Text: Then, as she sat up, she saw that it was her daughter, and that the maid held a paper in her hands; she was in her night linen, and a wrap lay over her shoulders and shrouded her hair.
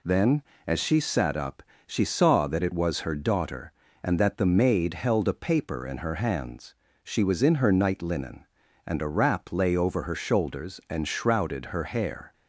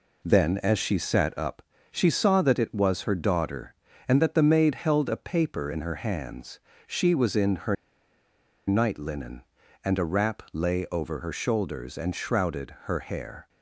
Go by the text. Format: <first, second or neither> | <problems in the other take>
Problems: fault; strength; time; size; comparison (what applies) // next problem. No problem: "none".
first | pauses between "her" and "night"; noticeable; at 7.7 s; 0.93 s long